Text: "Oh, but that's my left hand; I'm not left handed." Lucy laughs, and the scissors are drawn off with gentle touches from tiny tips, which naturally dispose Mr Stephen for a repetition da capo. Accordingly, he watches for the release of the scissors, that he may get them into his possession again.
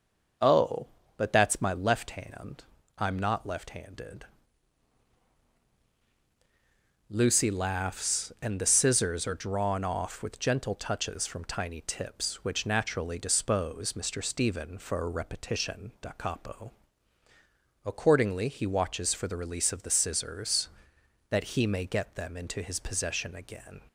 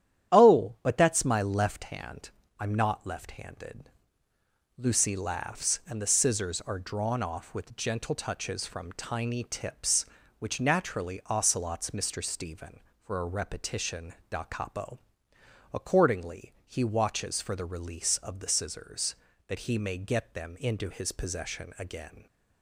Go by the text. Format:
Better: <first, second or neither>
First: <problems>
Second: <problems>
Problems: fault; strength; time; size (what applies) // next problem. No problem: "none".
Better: first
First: starts louder than the rest; noticeable; until 1.7 s; 6 dB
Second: starts louder than the rest; strong; until 1.3 s; 11 dB // says "ocelots" for "dispose"; at 11.2 s